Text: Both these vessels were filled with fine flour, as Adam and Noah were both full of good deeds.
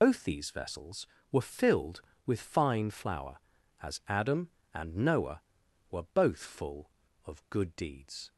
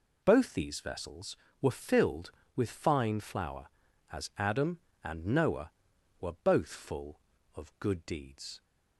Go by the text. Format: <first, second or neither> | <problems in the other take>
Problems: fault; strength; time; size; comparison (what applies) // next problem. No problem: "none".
second | loses the start of "Both"; at 0.0 s; 65 ms